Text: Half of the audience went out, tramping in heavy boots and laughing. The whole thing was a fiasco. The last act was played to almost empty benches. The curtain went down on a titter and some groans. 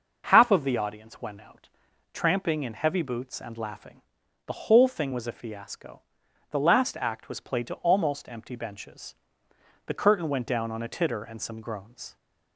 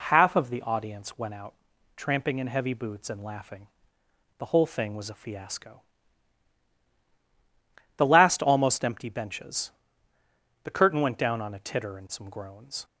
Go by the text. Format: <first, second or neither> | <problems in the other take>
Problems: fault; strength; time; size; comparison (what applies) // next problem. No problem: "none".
first | skips "act was played to"; at 8.4 s